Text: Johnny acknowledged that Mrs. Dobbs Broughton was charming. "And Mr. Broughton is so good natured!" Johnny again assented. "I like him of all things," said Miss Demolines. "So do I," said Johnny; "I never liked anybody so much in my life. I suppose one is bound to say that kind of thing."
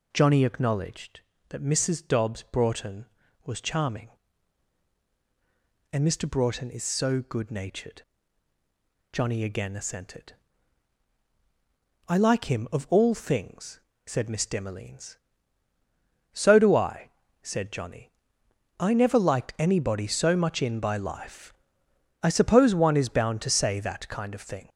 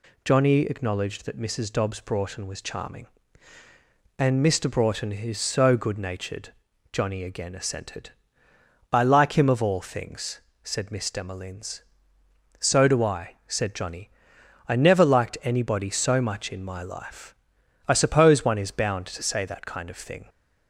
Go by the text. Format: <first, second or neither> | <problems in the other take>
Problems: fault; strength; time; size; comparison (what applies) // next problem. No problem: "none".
second | says "by" for "my"; at 20.8 s